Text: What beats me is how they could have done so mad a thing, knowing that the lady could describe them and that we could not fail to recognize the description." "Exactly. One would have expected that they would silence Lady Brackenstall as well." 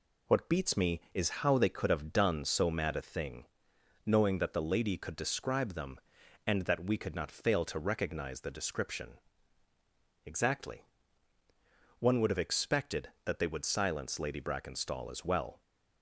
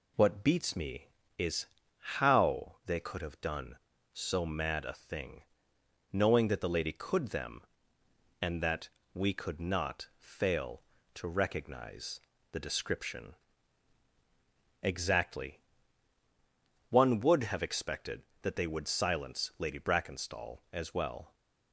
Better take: first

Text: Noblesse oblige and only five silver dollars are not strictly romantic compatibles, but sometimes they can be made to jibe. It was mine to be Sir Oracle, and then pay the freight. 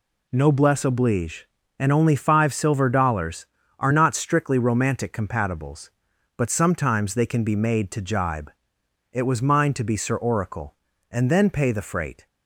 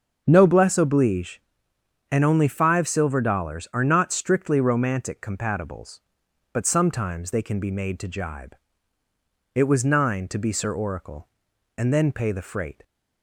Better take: first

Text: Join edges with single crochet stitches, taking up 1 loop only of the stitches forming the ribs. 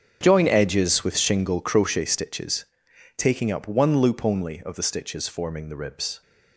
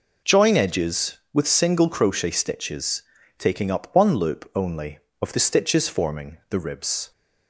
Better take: second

